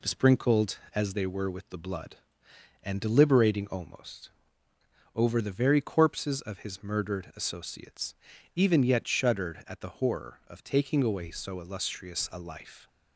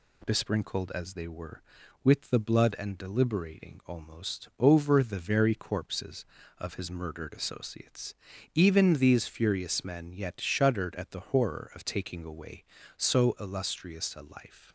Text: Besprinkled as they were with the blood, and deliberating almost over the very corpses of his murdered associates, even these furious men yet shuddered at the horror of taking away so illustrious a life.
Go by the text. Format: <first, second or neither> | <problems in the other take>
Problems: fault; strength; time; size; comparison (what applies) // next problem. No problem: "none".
second | pauses between "almost" and "over"; noticeable; at 4.2 s; 0.84 s long // skips "these furious men"; at 8.8 s